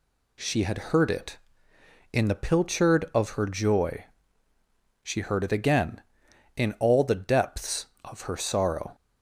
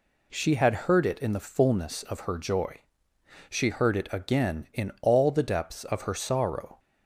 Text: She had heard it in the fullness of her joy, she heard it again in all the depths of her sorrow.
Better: second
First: says "pilchard" for "fullness"; at 2.4 s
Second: none

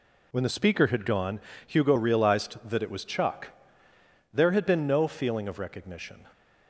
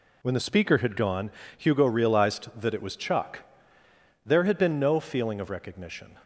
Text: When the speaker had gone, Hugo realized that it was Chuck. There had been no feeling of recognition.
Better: neither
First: none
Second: none

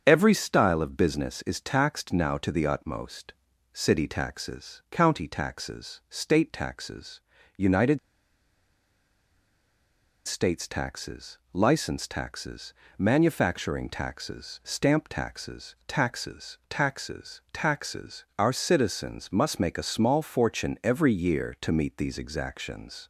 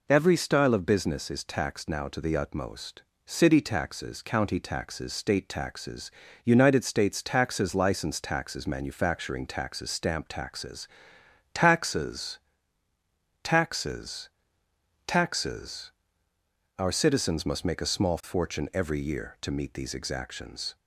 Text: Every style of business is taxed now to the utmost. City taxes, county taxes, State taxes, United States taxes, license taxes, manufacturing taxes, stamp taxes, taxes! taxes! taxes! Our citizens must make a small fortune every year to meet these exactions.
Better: second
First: starts louder than the rest; strong; until 1.0 s; 7.5 dB // pauses between "United" and "States"; strong; at 7.9 s; 2.2 s long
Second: none

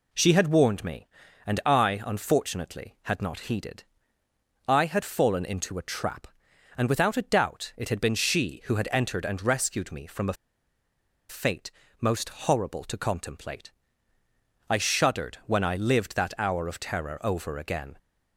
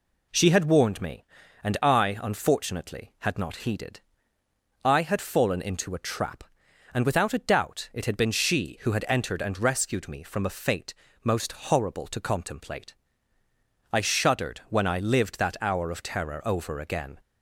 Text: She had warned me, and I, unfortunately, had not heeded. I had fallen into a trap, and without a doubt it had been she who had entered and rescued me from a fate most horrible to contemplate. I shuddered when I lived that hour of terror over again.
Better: second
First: pauses between "a" and "fate"; noticeable; at 10.3 s; 0.96 s long // pauses between "fate" and "most"; slight; at 11.7 s; 0.30 s long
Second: pauses between "fate" and "most"; slight; at 10.9 s; 0.30 s long

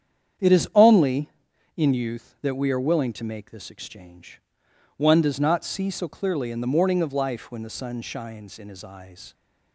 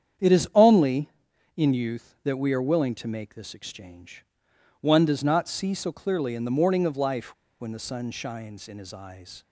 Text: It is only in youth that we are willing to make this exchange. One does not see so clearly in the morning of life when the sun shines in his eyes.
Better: first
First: starts louder than the rest; strong; until 1.9 s; 8.5 dB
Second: starts louder than the rest; strong; until 1.7 s; 8.5 dB // pauses between "life" and "when"; slight; at 7.3 s; 0.26 s long

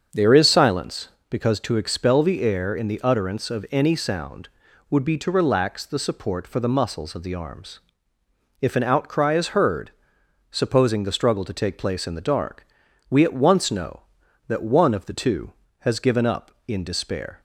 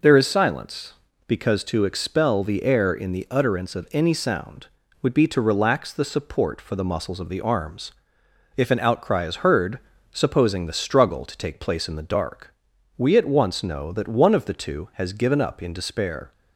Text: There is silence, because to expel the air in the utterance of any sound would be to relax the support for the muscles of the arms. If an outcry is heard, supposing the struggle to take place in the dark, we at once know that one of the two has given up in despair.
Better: second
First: starts louder than the rest; until 1.7 s; 7 dB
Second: none

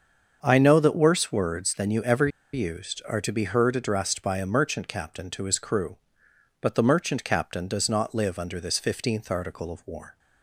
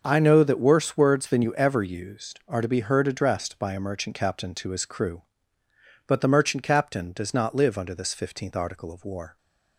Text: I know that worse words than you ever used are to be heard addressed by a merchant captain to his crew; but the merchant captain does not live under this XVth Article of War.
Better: second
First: starts louder than the rest; until 1.4 s; 6.5 dB // pauses between "ever" and "used"; slight; at 2.2 s; 0.25 s long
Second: starts louder than the rest; until 1.0 s; 6.5 dB

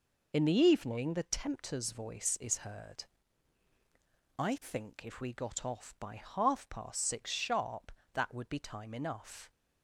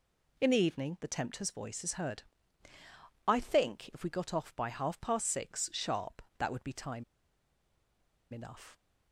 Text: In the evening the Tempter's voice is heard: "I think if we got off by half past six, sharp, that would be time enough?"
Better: first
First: none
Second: pauses between "time" and "enough"; strong; at 7.0 s; 1.2 s long

